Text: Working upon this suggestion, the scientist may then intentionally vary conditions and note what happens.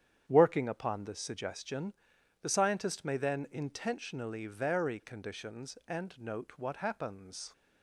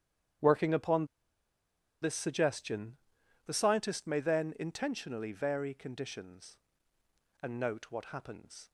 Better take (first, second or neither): first